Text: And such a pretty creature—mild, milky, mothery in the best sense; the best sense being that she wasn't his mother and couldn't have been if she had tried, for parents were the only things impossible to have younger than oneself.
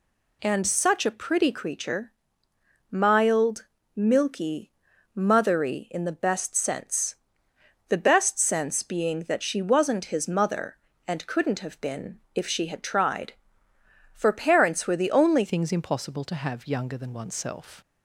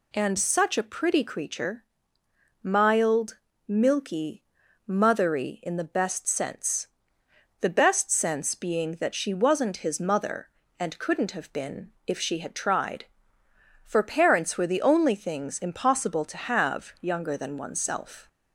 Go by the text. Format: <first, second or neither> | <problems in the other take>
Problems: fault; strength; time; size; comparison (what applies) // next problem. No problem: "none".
second | changes voice at "things"; from 15.4 s on; 2.4 s long